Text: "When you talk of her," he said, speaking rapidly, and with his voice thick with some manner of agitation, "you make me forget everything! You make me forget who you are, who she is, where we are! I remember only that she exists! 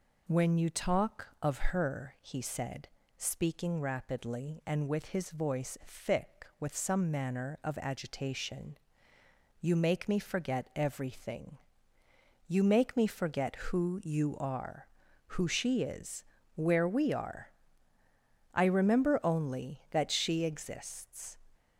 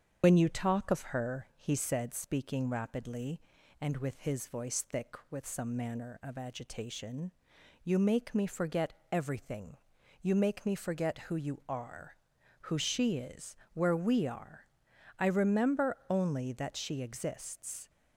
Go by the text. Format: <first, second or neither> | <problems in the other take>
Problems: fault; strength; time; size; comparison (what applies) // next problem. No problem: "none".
first | loses the start of "When"; at 0.2 s; 90 ms // starts louder than the rest; strong; until 1.2 s; 7.5 dB // pauses between "forget" and "everything"; slight; at 8.9 s; 0.18 s long